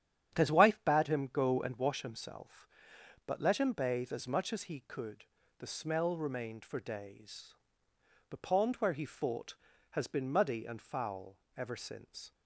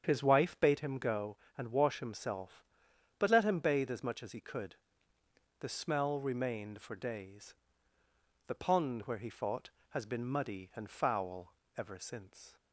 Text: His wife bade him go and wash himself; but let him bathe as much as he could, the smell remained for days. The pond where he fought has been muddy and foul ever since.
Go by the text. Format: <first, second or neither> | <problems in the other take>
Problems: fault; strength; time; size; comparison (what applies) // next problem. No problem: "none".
neither | starts louder than the rest; strong; the same in both // pauses between "foul" and "ever"; slight; the same in both